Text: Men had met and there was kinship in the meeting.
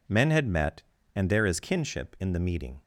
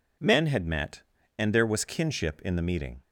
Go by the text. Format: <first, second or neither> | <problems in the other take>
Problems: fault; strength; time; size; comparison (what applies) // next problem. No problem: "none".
second | says "is" for "was"; at 1.4 s